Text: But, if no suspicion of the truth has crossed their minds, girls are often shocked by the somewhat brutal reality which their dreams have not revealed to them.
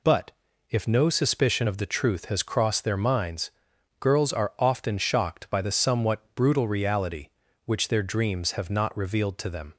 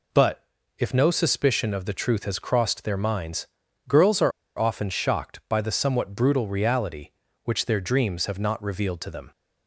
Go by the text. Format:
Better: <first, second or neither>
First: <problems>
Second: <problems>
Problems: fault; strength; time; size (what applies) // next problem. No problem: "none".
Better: first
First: none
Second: pauses between "are" and "often"; slight; at 4.3 s; 0.27 s long